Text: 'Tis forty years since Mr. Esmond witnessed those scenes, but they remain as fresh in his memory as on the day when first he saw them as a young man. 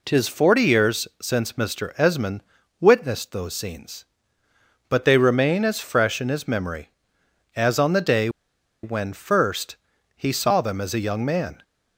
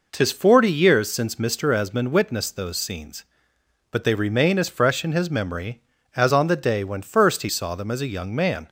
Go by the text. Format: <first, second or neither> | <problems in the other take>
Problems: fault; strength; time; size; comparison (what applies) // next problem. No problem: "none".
second | pauses between "Esmond" and "witnessed"; slight; at 2.4 s; 0.36 s long // pauses between "day" and "when"; noticeable; at 8.2 s; 0.54 s long // pauses between "first" and "he"; at 9.7 s; 0.40 s long